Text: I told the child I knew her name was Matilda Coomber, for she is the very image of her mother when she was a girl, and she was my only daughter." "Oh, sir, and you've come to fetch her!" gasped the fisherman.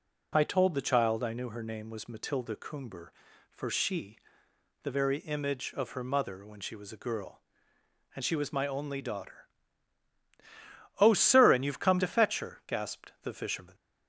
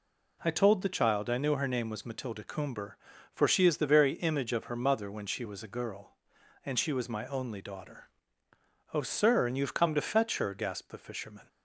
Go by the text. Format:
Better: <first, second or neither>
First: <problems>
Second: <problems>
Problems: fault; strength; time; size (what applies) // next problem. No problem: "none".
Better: second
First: skips "is"; at 4.4 s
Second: none